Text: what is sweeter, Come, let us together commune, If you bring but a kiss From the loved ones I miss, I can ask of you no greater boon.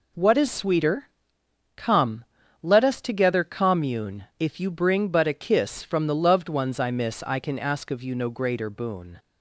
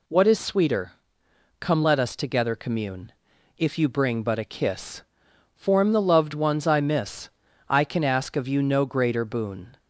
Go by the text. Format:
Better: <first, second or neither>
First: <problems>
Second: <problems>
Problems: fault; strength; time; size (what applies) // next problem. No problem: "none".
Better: first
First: none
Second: says "Form" for "From"; at 5.5 s